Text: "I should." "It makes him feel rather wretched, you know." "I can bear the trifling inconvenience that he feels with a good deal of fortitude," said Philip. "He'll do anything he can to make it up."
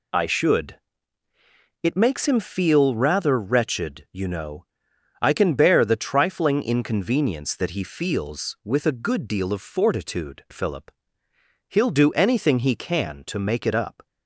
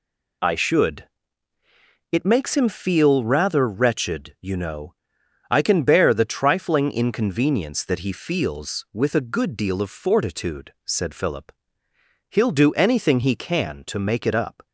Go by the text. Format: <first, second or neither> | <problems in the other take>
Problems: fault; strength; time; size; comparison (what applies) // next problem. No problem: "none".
second | skips "said"; at 10.4 s